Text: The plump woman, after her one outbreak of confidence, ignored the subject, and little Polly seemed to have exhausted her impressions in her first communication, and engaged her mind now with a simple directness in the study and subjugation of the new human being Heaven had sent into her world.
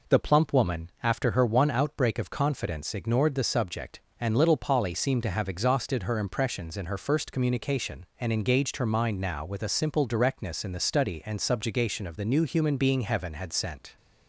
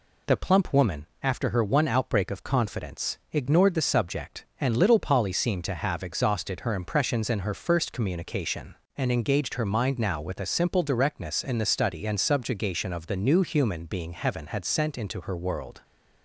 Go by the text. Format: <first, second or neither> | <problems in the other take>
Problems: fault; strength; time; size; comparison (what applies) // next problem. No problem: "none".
second | stops before "into her world"; at 13.9 s